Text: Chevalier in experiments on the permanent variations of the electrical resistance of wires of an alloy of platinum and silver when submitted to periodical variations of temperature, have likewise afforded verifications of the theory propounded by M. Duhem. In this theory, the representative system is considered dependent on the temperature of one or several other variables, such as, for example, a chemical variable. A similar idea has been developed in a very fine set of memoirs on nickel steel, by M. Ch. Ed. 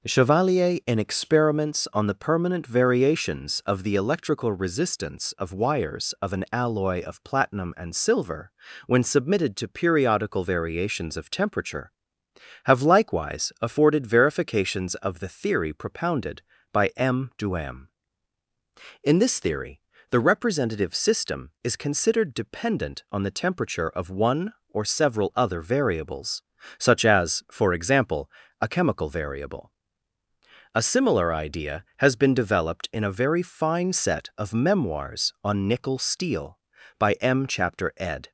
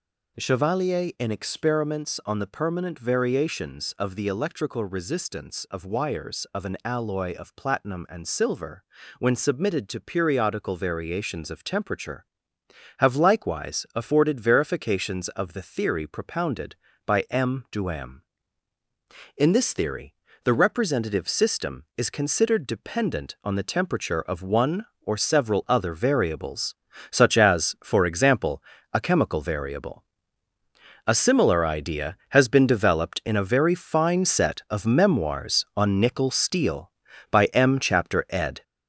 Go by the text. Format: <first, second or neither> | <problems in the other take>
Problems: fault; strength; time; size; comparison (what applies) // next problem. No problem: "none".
first | gets louder; noticeable; throughout; 5 dB // pauses between "silver" and "when"; at 8.8 s; 0.38 s long; also in the first